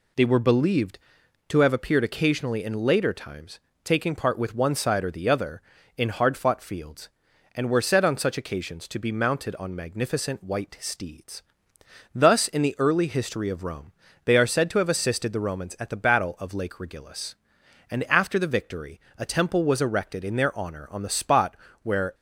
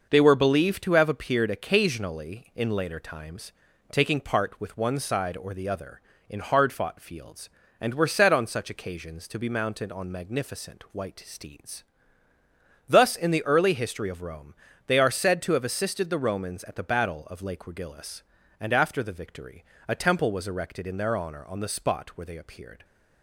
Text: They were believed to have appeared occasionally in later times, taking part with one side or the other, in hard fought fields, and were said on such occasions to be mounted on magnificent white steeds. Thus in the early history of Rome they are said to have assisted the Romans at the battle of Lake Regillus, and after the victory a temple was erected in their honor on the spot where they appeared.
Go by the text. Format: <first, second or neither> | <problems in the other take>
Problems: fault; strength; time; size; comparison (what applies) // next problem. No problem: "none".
second | pauses between "Rome" and "they"; slight; at 13.9 s; 0.32 s long; slight in the second // pauses between "victory" and "a"; slight; at 18.9 s; 0.18 s long; slight in the second // pauses between "spot" and "where"; slight; at 21.5 s; 0.26 s long // stops before "they appeared"; at 22.1 s